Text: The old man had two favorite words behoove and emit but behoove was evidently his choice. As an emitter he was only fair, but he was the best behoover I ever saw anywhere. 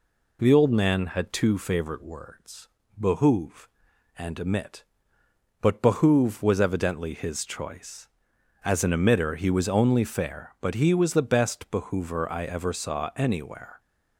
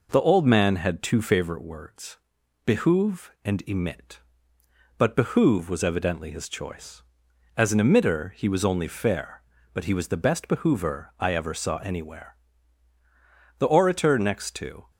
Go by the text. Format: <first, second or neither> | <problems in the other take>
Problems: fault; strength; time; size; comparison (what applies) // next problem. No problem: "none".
first | pauses between "words" and "behoove"; noticeable; at 2.1 s; 0.50 s long; slight in the first // goes on to say "The orator next to"; from 13.5 s on; 1.3 s long